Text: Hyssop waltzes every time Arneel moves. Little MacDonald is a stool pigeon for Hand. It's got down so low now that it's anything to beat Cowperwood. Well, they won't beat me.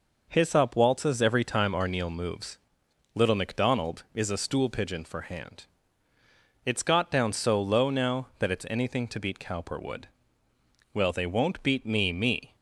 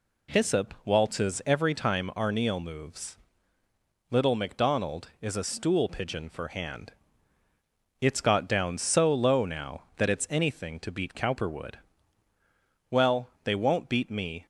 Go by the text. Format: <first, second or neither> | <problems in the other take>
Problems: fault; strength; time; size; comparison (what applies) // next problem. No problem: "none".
second | says "me" twice; at 12.1 s